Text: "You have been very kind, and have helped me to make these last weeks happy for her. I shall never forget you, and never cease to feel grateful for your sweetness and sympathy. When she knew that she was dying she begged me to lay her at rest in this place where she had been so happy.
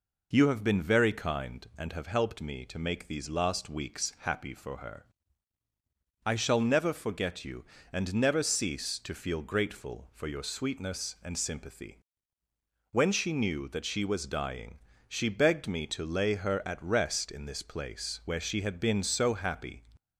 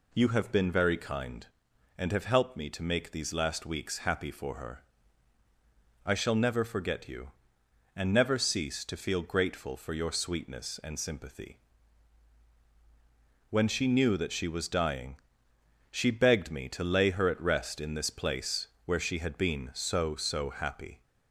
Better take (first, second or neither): first